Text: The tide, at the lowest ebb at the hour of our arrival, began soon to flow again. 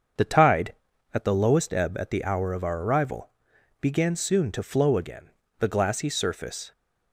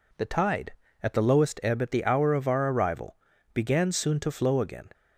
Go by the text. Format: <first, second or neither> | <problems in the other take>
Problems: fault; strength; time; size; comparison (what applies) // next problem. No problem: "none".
second | starts louder than the rest; until 1.6 s; 7 dB // goes on to say "The glassy surface"; noticeable; from 5.5 s on; 1.1 s long